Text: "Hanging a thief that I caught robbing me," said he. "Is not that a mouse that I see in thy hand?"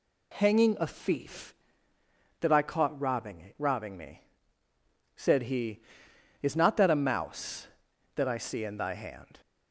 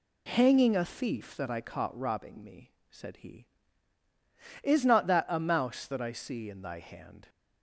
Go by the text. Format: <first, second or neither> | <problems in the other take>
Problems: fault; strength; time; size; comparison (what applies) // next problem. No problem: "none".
second | says "robbing" twice; at 3.5 s